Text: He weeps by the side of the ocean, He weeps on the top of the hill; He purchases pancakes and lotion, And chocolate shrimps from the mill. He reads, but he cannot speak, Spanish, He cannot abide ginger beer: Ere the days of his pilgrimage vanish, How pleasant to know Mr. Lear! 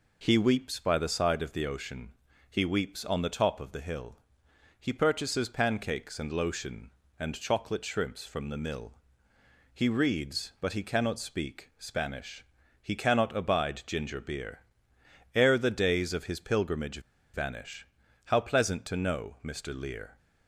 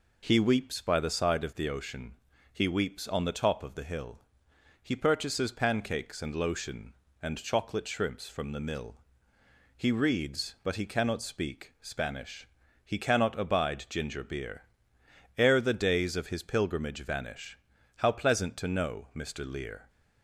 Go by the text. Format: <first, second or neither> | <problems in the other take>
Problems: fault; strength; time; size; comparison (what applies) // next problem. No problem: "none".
second | pauses between "pilgrimage" and "vanish"; slight; at 16.9 s; 0.33 s long